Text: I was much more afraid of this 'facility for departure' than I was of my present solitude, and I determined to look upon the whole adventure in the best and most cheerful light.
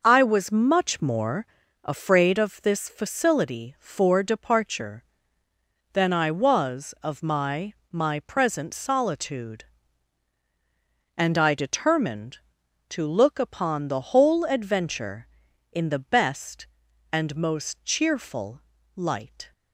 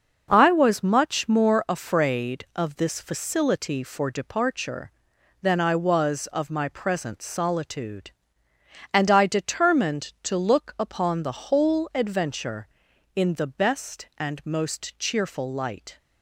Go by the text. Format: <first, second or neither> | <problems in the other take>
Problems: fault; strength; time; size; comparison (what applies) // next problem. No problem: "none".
second | pauses between "more" and "afraid"; at 1.4 s; 0.38 s long // says "my" twice; at 7.9 s // pauses between "cheerful" and "light"; slight; at 18.5 s; 0.36 s long